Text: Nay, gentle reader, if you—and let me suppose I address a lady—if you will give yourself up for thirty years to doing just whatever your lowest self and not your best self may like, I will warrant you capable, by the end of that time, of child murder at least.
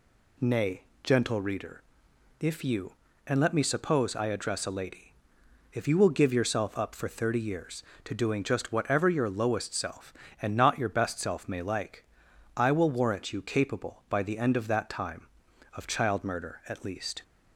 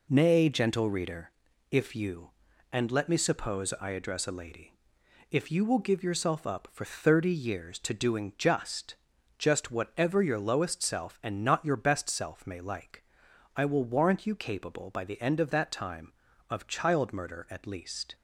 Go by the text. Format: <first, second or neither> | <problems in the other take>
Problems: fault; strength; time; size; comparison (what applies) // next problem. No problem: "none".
first | says "just" twice; at 9.3 s